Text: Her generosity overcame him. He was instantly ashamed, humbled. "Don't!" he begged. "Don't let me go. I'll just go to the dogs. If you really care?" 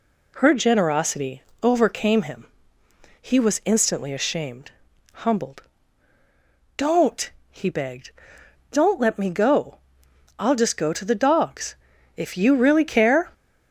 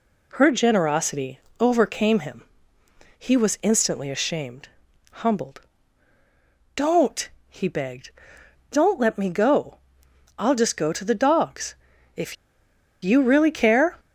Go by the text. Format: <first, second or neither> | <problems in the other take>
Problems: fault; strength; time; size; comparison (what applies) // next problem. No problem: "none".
first | pauses between "generosity" and "overcame"; slight; at 1.3 s; 0.20 s long; slight in the first // pauses between "If" and "you"; noticeable; at 12.3 s; 0.69 s long